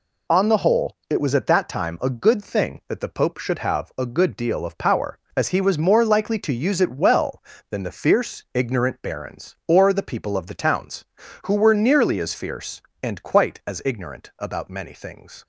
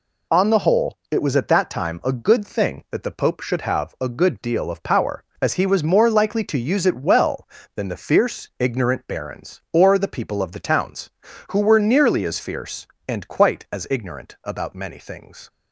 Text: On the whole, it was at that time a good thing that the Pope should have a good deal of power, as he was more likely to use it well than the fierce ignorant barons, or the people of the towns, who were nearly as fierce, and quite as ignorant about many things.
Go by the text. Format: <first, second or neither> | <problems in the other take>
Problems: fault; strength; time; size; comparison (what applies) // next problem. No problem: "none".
neither | none